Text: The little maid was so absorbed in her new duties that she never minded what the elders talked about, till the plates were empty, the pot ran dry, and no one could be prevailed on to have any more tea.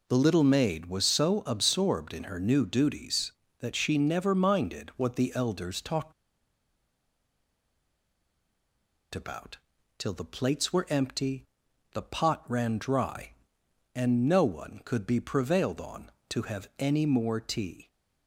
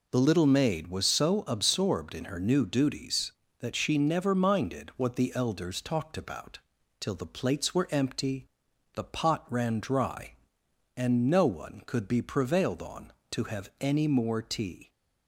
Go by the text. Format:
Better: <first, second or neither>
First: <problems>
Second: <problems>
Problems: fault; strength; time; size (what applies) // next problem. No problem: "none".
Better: second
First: pauses between "talked" and "about"; strong; at 6.1 s; 3.0 s long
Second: none